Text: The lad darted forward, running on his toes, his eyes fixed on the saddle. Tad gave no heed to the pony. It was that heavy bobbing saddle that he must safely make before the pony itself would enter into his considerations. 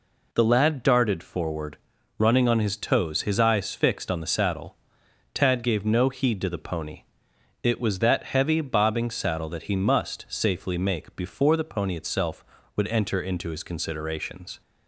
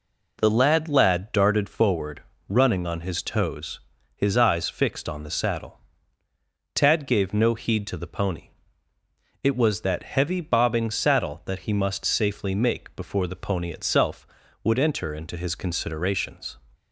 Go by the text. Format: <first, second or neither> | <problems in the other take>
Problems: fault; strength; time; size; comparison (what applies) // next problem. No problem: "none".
first | says "lad" twice; at 0.8 s